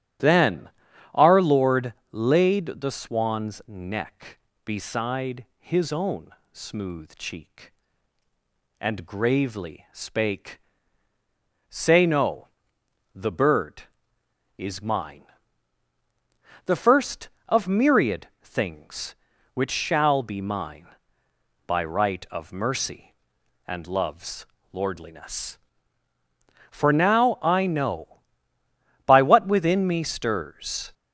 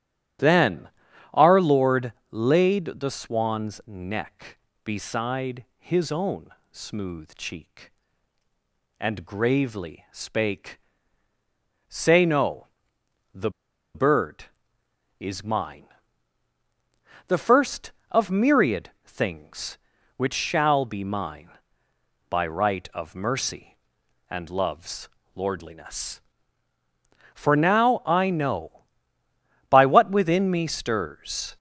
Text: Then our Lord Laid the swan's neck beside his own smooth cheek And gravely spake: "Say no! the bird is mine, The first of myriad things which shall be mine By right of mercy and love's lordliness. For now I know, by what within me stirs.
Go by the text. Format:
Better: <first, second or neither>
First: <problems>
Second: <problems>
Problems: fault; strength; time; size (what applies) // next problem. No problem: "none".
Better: first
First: starts louder than the rest; strong; until 1.6 s; 12.5 dB // pauses between "Then" and "our"; noticeable; at 0.6 s; 0.46 s long // pauses between "Lord" and "Laid"; slight; at 1.9 s; 0.20 s long // pauses between "own" and "smooth"; slight; at 6.2 s; 0.24 s long // pauses between "myriad" and "things"; slight; at 18.2 s; 0.16 s long // pauses between "love's" and "lordliness"; slight; at 24.4 s; 0.30 s long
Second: starts louder than the rest; strong; until 1.8 s; 12.5 dB // pauses between "Then" and "our"; noticeable; at 0.8 s; 0.46 s long // pauses between "Lord" and "Laid"; slight; at 2.1 s; 0.20 s long // pauses between "own" and "smooth"; slight; at 6.4 s; 0.24 s long // pauses between "the" and "bird"; at 13.5 s; 0.44 s long // pauses between "myriad" and "things"; slight; at 18.8 s; 0.16 s long // pauses between "love's" and "lordliness"; slight; at 25.0 s; 0.30 s long